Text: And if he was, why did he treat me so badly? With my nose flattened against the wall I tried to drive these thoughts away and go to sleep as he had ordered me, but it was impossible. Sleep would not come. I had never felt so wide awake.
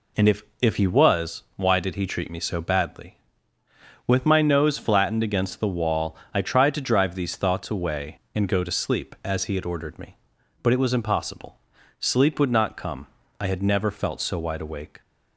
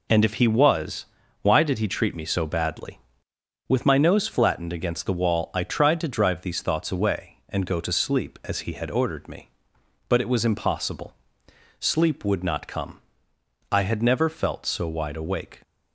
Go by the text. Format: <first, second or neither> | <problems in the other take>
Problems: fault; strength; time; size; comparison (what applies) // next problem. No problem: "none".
second | says "if" twice; at 0.6 s // pauses between "wall" and "I"; slight; at 6.1 s; 0.18 s long